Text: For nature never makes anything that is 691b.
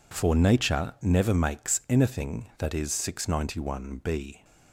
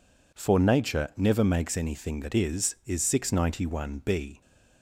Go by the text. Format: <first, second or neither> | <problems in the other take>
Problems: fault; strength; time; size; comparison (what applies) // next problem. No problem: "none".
first | says "is" twice; at 2.8 s